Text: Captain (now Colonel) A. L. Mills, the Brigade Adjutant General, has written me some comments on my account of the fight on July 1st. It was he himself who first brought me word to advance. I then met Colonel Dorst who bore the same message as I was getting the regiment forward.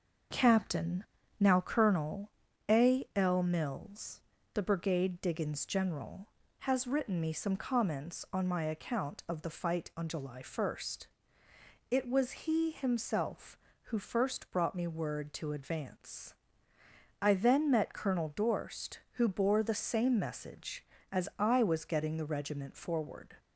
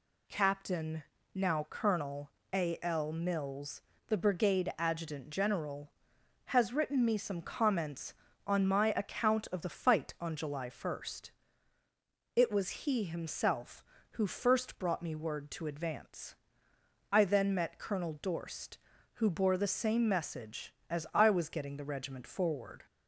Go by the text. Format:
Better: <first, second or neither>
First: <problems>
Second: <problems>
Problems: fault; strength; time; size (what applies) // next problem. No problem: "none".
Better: second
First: starts louder than the rest; noticeable; until 1.6 s; 6 dB // says "Diggins" for "Adjutant"; at 5.1 s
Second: none